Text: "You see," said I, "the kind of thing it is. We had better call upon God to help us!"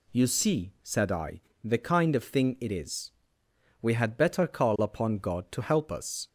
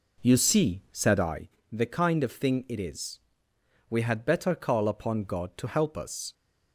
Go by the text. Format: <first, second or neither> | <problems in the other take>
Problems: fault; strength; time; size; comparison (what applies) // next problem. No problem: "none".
first | starts louder than the rest; until 1.5 s; 4 dB